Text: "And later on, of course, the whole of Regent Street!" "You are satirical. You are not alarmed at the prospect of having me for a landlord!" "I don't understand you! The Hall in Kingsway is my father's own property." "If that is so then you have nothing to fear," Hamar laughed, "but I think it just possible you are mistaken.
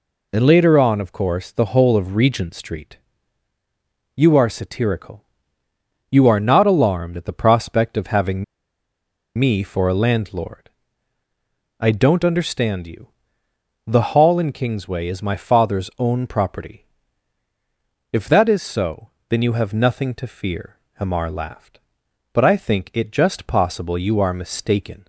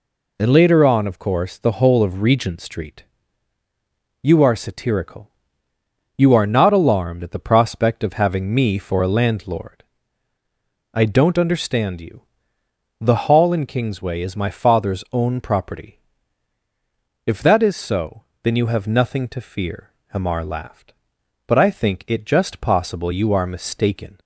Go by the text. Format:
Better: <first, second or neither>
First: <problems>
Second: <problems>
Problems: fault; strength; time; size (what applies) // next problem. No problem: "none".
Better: second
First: pauses between "having" and "me"; noticeable; at 8.4 s; 0.93 s long // pauses between "so" and "then"; slight; at 19.1 s; 0.18 s long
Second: pauses between "so" and "then"; slight; at 18.2 s; 0.18 s long